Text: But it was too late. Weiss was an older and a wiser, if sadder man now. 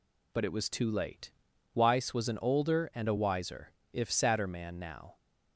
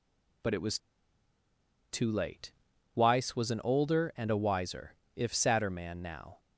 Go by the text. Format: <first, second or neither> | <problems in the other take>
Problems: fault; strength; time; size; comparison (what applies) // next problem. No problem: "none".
first | pauses between "was" and "too"; at 0.7 s; 1.1 s long